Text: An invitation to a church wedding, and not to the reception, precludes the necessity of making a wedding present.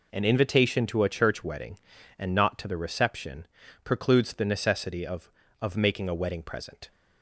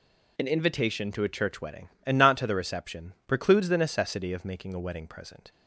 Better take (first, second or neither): second